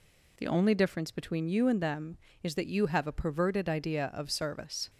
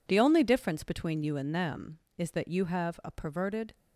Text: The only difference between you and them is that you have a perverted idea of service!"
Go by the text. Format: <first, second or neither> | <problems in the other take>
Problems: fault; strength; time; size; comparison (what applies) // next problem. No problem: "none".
first | stops before "idea of service"; at 3.7 s